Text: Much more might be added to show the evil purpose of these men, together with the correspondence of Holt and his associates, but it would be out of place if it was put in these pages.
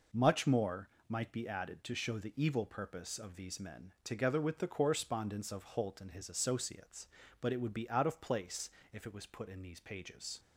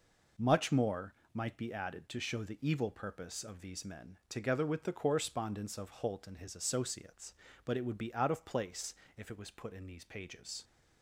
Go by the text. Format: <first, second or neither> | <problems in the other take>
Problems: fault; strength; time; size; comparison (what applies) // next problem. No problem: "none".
neither | pauses between "more" and "might"; slight; the same in both // pauses between "place" and "if"; slight; the same in both